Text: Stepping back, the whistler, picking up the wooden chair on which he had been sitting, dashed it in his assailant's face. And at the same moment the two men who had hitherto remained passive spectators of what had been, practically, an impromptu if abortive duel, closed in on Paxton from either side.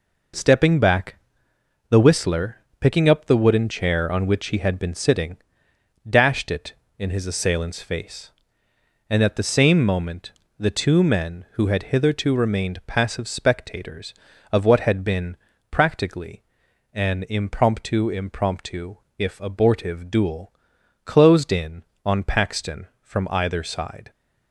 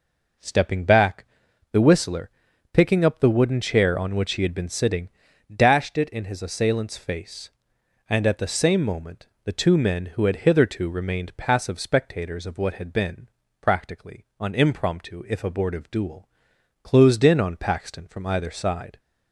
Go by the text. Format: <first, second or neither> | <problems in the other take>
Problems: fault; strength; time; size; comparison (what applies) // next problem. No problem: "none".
second | pauses between "moment" and "the"; slight; at 10.3 s; 0.26 s long; slight in the second // says "impromptu" twice; at 18.0 s